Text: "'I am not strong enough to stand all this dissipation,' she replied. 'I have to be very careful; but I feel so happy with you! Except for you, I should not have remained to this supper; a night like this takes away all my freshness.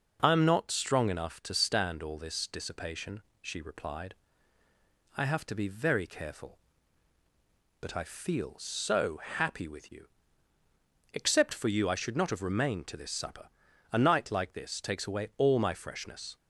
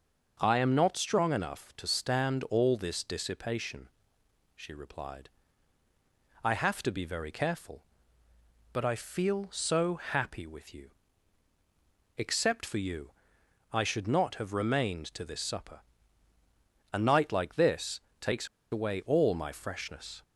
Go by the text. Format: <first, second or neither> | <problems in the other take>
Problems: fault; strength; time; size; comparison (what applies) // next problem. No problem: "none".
first | starts louder than the rest; until 1.4 s; 6 dB // pauses between "this" and "takes"; slight; at 17.9 s; 0.22 s long // pauses between "takes" and "away"; slight; at 18.4 s; 0.25 s long